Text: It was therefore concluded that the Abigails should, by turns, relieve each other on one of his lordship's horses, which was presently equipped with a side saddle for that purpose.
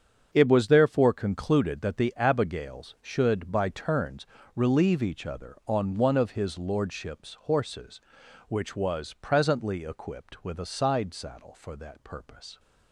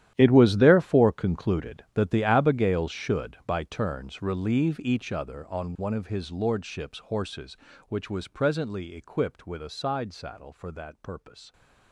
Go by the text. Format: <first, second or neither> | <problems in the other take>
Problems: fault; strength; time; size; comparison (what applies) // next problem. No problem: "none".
first | gets quieter; strong; throughout; 17 dB // starts louder than the rest; strong; until 1.1 s; 11.5 dB; strong in the first